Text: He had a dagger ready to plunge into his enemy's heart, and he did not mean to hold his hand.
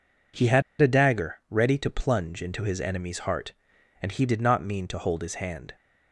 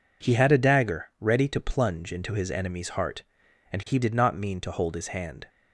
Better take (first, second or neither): second